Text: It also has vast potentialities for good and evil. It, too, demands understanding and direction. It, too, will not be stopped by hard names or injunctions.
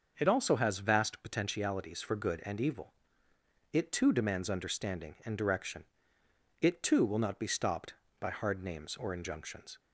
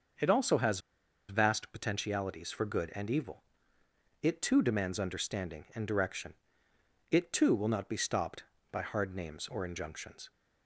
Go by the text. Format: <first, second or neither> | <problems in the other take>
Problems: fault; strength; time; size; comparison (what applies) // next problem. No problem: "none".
first | starts louder than the rest; until 1.6 s; 6 dB // pauses between "has" and "vast"; noticeable; at 0.7 s; 0.49 s long